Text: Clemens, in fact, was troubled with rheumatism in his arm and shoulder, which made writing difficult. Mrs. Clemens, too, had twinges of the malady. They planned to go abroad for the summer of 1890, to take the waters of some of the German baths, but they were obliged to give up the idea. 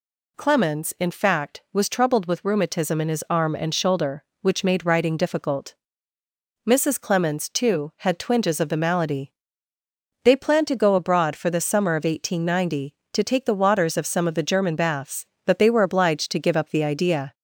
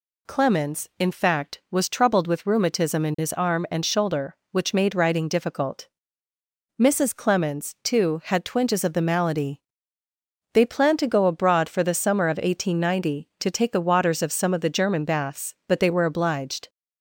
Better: first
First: none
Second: stops before "to give up the idea"; at 16.6 s

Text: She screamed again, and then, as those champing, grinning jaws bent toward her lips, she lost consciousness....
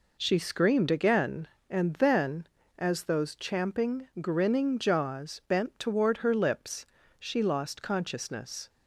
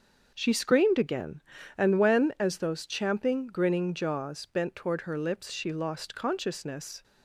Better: first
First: none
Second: starts louder than the rest; until 1.3 s; 6.5 dB // says "when" for "then"; at 1.9 s

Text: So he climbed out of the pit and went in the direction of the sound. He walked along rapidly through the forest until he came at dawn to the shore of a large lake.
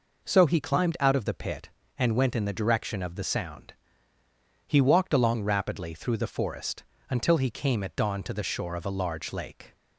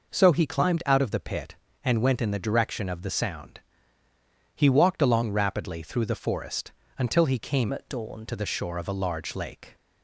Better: first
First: pauses between "forest" and "until"; slight; at 6.8 s; 0.26 s long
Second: pauses between "forest" and "until"; slight; at 6.7 s; 0.26 s long // changes voice from "at" to "dawn"; from 7.7 to 8.2 s; 0.5 s long

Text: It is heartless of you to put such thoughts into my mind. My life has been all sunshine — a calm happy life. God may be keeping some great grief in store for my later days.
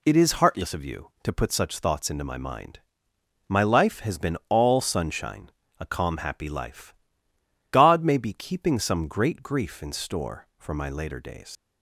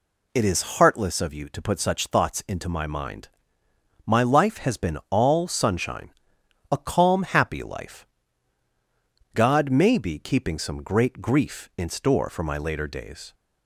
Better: second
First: leaves "days" unfinished; at 11.5 s; 70 ms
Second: none

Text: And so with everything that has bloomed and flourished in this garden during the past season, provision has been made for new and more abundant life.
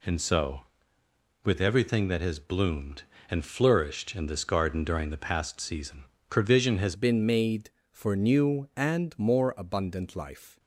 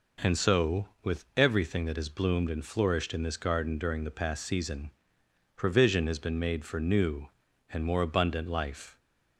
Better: second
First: changes voice at "been"; from 6.9 s on; 3.6 s long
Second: none

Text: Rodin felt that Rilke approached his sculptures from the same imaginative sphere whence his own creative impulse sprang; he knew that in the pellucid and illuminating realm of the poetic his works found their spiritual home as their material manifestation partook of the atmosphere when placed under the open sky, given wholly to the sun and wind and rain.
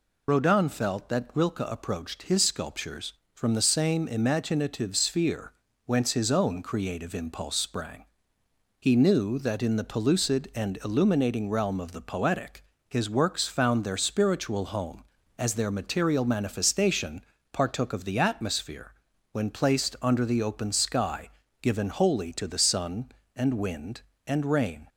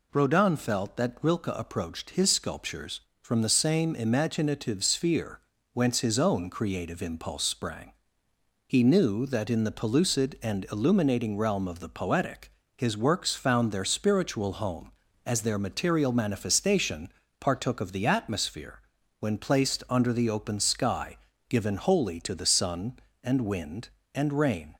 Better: second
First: loses the start of "Rodin"; at 0.2 s; 40 ms // pauses between "sphere" and "whence"; slight; at 5.5 s; 0.32 s long // pauses between "poetic" and "his"; slight; at 12.6 s; 0.26 s long // pauses between "manifestation" and "partook"; slight; at 17.2 s; 0.26 s long // pauses between "atmosphere" and "when"; at 18.9 s; 0.40 s long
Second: pauses between "sphere" and "whence"; slight; at 5.3 s; 0.32 s long // pauses between "poetic" and "his"; slight; at 12.4 s; 0.26 s long // pauses between "manifestation" and "partook"; slight; at 17.1 s; 0.26 s long // pauses between "atmosphere" and "when"; at 18.7 s; 0.40 s long

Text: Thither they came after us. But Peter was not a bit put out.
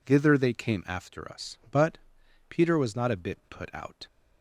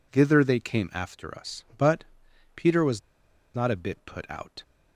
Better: first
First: pauses between "But" and "Peter"; noticeable; at 1.9 s; 0.50 s long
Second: pauses between "But" and "Peter"; noticeable; at 2.0 s; 0.50 s long // pauses between "was" and "not"; noticeable; at 3.0 s; 0.55 s long

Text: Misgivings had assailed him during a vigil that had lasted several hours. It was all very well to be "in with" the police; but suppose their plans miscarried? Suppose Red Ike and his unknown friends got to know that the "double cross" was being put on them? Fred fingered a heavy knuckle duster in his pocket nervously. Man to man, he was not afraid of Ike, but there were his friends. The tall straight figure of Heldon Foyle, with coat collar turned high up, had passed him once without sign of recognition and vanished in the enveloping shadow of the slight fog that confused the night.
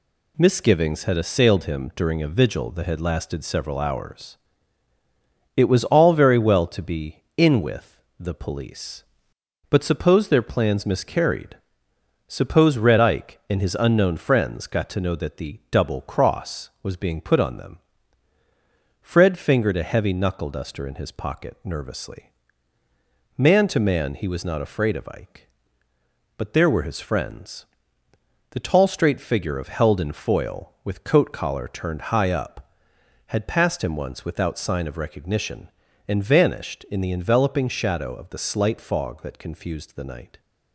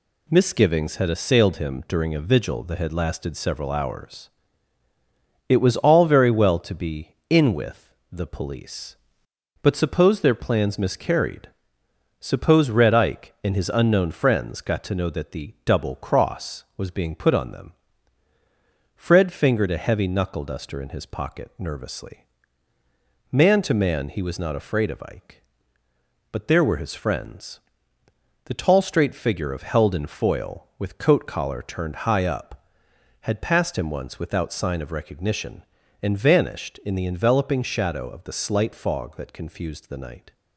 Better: neither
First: pauses between "with" and "the"; slight; at 7.9 s; 0.18 s long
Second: pauses between "with" and "the"; slight; at 7.9 s; 0.18 s long

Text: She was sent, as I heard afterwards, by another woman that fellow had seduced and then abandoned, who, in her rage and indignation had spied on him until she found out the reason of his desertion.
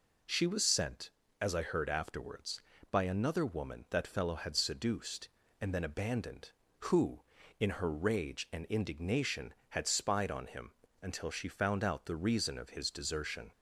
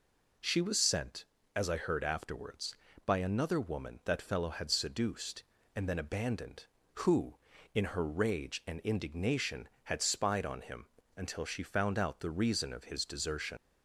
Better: first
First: pauses between "him" and "until"; slight; at 10.7 s; 0.26 s long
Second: pauses between "him" and "until"; slight; at 10.8 s; 0.26 s long // leaves "desertion" unfinished; at 13.5 s; 90 ms

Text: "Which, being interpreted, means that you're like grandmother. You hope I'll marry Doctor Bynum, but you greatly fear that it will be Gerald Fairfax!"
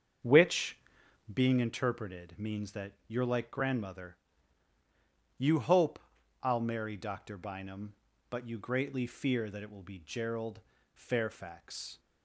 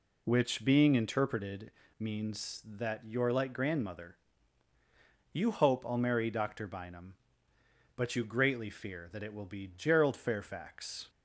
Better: second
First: starts louder than the rest; strong; until 1.5 s; 7 dB // pauses between "hope" and "I'll"; noticeable; at 5.9 s; 0.46 s long // pauses between "Gerald" and "Fairfax"; slight; at 10.5 s; 0.34 s long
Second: none

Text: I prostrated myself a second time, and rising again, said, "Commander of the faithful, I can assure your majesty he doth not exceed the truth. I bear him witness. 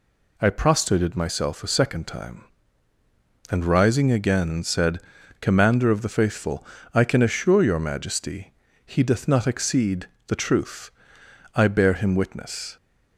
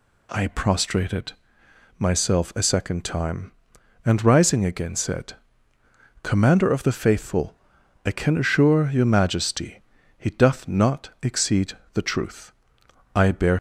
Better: first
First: pauses between "majesty" and "he"; slight; at 8.5 s; 0.32 s long // pauses between "exceed" and "the"; slight; at 10.0 s; 0.20 s long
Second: pauses between "prostrated" and "myself"; noticeable; at 1.3 s; 0.66 s long // pauses between "majesty" and "he"; slight; at 9.8 s; 0.36 s long // pauses between "exceed" and "the"; slight; at 11.7 s; 0.22 s long // stops before "him witness"; at 13.5 s

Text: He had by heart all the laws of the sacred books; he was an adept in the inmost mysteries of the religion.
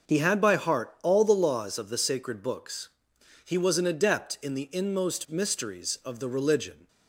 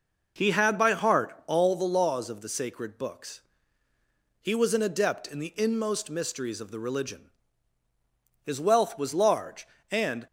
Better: first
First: none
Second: goes on to say "His wealth was large and"; strong; from 8.4 s on; 1.8 s long

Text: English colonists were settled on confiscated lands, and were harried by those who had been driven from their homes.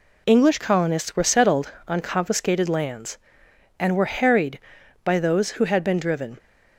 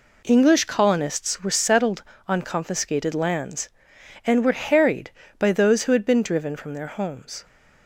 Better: second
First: stops before "from their homes"; at 6.3 s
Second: none

